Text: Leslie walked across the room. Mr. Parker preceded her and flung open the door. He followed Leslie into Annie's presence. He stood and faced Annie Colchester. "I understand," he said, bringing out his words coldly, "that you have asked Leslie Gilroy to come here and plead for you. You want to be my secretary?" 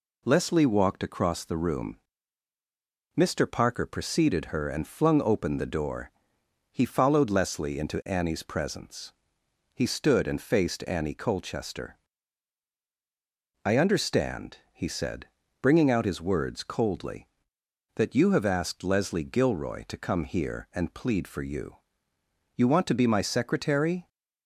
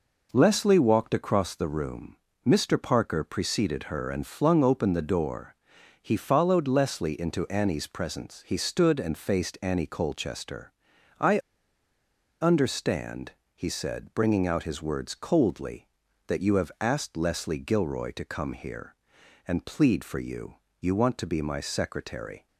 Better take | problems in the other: first | pauses between "I" and "understand"; at 11.3 s; 1.0 s long

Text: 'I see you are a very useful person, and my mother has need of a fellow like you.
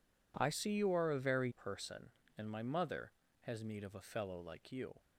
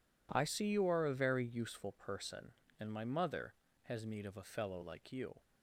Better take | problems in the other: second | skips "useful"; at 1.4 s

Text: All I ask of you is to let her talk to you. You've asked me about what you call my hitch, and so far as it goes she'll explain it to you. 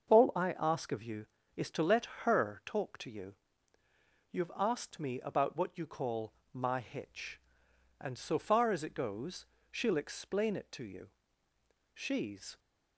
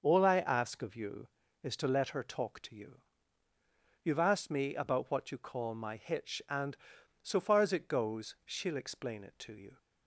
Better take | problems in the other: second | starts louder than the rest; until 1.1 s; 7 dB; noticeable in the second // pauses between "let" and "her"; slight; at 2.0 s; 0.16 s long // pauses between "call" and "my"; slight; at 6.3 s; 0.20 s long // pauses between "goes" and "she'll"; slight; at 9.4 s; 0.26 s long // goes on to say "She's"; noticeable; from 11.9 s on; 0.66 s long

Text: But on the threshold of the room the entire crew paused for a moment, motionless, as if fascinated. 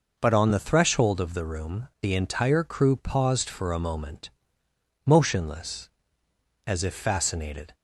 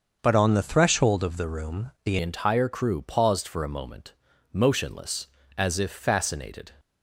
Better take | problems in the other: first | starts louder than the rest; until 1.2 s; 6.5 dB // changes voice at "entire"; from 2.2 s on; 4.5 s long

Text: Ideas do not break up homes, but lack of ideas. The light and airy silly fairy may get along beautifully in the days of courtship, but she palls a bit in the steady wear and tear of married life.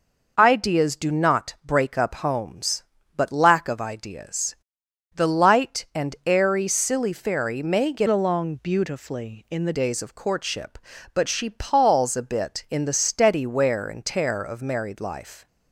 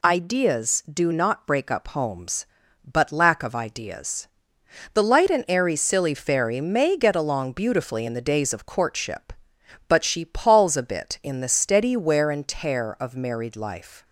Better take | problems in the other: second | changes voice from "along" to "the"; from 8.0 to 9.7 s; 1.7 s long

